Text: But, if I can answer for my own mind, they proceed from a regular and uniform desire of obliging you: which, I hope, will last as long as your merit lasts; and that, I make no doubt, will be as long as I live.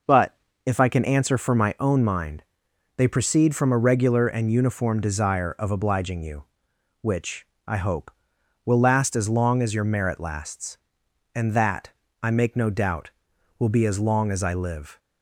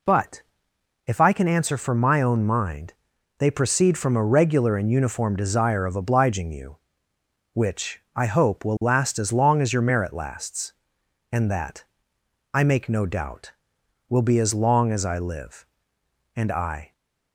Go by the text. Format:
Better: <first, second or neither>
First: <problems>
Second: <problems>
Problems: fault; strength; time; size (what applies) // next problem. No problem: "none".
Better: first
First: none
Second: goes on to say "And I"; from 16.3 s on; 0.56 s long